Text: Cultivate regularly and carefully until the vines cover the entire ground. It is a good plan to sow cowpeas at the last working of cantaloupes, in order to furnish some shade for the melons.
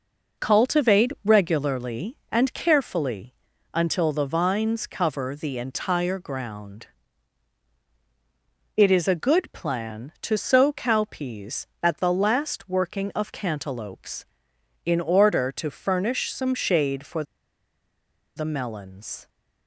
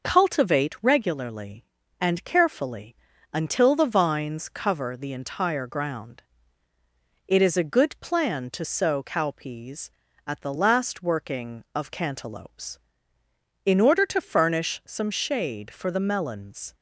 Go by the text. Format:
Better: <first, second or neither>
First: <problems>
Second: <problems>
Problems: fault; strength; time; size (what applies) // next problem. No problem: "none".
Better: second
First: pauses between "carefully" and "until"; at 3.3 s; 0.40 s long // pauses between "for" and "the"; at 17.2 s; 1.1 s long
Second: pauses between "carefully" and "until"; slight; at 2.9 s; 0.36 s long